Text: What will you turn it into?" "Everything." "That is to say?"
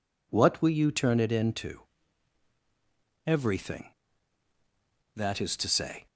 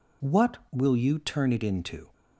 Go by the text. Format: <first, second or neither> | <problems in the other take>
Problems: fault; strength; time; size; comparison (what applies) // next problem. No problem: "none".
first | stops before "Everything That is to say"; at 2.1 s